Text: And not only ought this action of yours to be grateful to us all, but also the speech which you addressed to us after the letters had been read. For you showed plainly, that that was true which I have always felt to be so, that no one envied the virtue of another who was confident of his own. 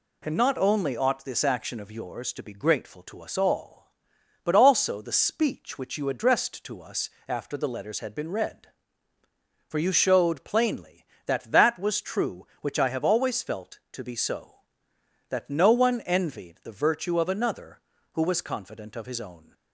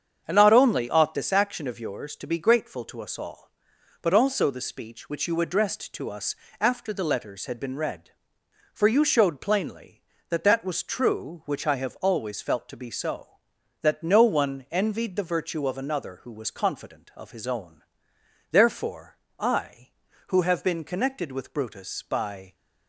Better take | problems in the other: first | starts louder than the rest; strong; until 1.2 s; 7.5 dB // pauses between "us" and "after"; slight; at 6.3 s; 0.24 s long; slight in the first // goes on to say "Therefore I who have been connected with Brutus by"; strong; from 18.4 s on; 4.0 s long

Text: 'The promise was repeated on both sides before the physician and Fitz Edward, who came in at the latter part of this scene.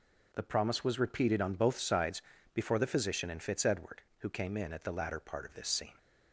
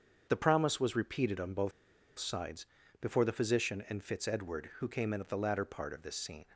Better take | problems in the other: first | starts louder than the rest; until 1.3 s; 7 dB // pauses between "both" and "sides"; noticeable; at 1.7 s; 0.46 s long // pauses between "sides" and "before"; slight; at 2.6 s; 0.34 s long; slight in the first

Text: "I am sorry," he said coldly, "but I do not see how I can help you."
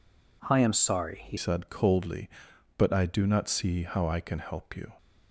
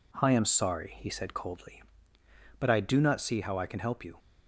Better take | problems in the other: second | changes voice at "said"; from 1.3 s on; 3.6 s long

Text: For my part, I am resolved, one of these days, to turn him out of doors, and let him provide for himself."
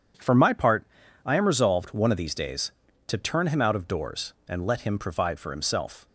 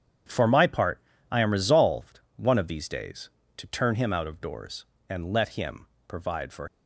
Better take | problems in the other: first | starts louder than the rest; strong; until 1.5 s; 8.5 dB // pauses between "him" and "provide"; slight; at 5.8 s; 0.20 s long // stops before "himself"; at 6.6 s

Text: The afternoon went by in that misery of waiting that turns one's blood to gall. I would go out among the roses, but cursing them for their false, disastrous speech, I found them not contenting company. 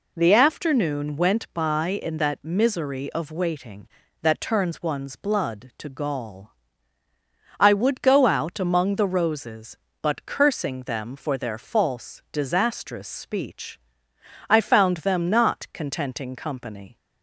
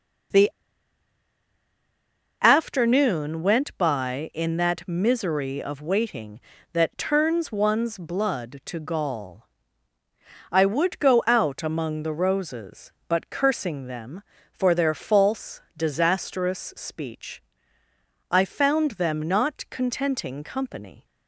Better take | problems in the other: first | pauses between "The" and "afternoon"; strong; at 0.4 s; 1.9 s long

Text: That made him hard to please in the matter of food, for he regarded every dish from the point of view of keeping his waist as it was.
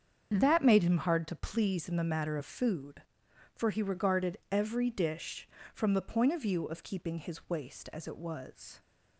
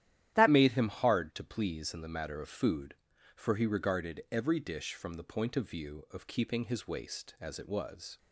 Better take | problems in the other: first | starts louder than the rest; strong; until 1.3 s; 12 dB; strong in the first // changes voice at "made"; from 0.4 s on; 7.7 s long

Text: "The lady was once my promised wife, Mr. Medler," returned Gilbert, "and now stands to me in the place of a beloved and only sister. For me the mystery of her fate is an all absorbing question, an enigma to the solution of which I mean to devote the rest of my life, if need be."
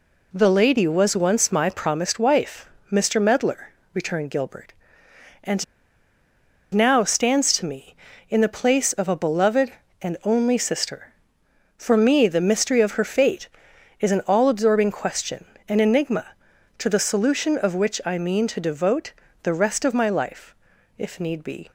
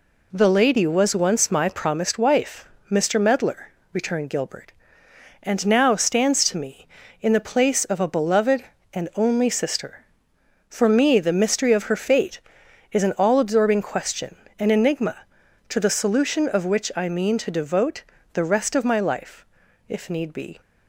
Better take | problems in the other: second | pauses between "and" and "now"; at 5.6 s; 1.0 s long // pauses between "devote" and "the"; slight; at 19.1 s; 0.32 s long; slight in the second

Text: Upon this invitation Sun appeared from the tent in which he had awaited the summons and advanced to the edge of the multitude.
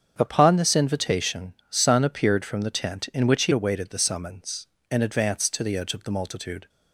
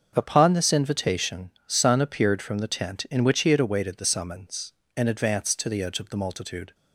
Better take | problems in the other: second | starts louder than the rest; strong; until 1.1 s; 7.5 dB; also in the second // pauses between "invitation" and "Sun"; slight; at 1.5 s; 0.16 s long; slight in the second // skips "had"; at 3.5 s

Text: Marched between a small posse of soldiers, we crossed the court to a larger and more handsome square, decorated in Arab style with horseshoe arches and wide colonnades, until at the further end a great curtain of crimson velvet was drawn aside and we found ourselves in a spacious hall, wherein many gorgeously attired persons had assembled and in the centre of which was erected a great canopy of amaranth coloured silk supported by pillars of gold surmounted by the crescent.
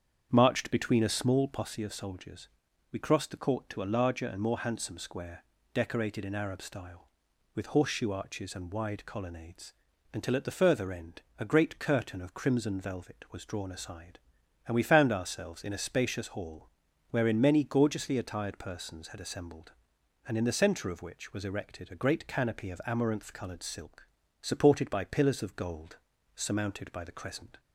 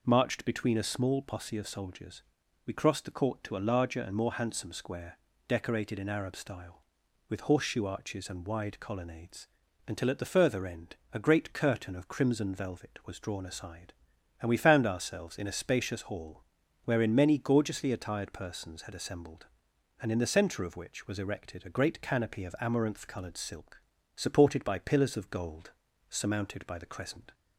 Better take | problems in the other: second | starts louder than the rest; strong; until 1.7 s; 7.5 dB // pauses between "end" and "a"; slight; at 11.2 s; 0.16 s long; slight in the second // pauses between "silk" and "supported"; at 24.0 s; 0.38 s long; also in the second // pauses between "gold" and "surmounted"; at 25.9 s; 0.38 s long; also in the second

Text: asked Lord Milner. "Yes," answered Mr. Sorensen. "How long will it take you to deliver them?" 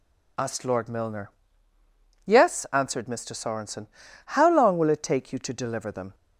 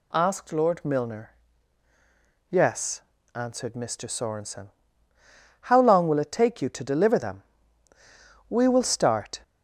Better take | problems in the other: first | goes on to say "We will start"; noticeable; from 8.4 s on; 0.90 s long

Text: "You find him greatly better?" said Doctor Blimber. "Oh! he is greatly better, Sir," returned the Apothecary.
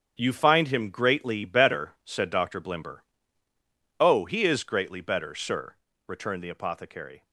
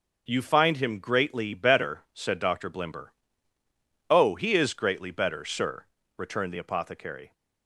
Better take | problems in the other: second | gets quieter; strong; throughout; 10 dB

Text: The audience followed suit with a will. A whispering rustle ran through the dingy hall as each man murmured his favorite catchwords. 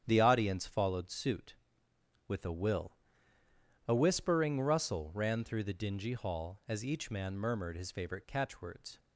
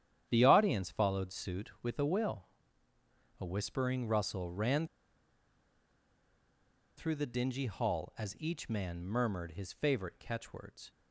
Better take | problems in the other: first | starts louder than the rest; strong; until 1.3 s; 10 dB; strong in the first // pauses between "ran" and "through"; strong; at 4.8 s; 2.1 s long

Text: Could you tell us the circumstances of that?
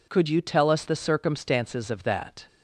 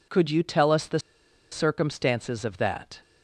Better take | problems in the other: first | pauses between "the" and "circumstances"; noticeable; at 0.9 s; 0.53 s long

